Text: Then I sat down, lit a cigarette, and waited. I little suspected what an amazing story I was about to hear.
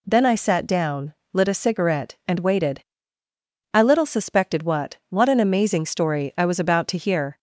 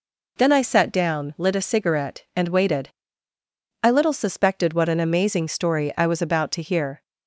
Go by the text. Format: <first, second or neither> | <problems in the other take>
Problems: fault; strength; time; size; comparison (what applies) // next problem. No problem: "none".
second | says "what" twice; at 5.0 s